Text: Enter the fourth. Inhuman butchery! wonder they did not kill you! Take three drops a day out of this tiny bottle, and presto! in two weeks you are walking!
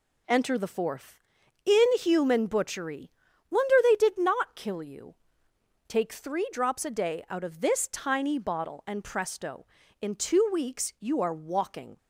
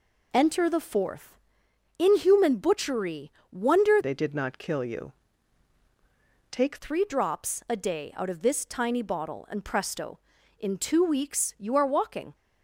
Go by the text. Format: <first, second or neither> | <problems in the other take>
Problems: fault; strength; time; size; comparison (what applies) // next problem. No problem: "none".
first | changes voice from "they" to "Take"; from 4.0 to 6.7 s; 2.7 s long